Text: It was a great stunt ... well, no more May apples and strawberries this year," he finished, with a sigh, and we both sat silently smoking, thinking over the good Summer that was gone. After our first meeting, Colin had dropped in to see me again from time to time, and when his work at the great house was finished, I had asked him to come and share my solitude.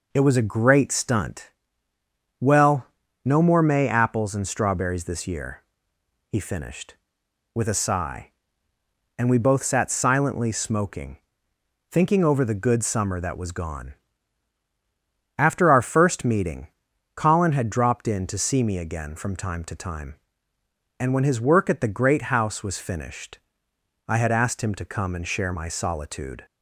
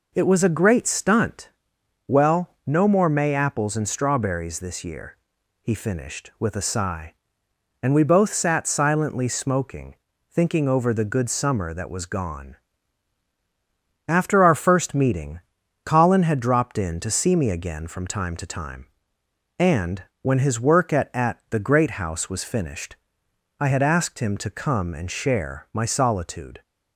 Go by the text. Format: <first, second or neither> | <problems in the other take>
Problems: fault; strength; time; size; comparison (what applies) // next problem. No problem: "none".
first | pauses between "and" and "when"; slight; at 20.0 s; 0.18 s long // says "at" twice; at 21.1 s